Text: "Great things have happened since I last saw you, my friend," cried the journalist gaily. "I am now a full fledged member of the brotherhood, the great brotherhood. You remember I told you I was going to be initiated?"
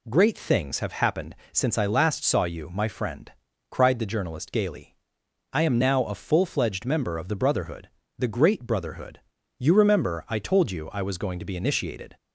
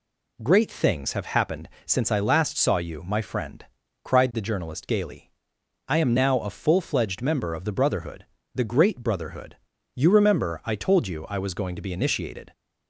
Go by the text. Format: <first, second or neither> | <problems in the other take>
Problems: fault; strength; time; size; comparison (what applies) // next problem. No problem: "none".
neither | pauses between "happened" and "since"; slight; the same in both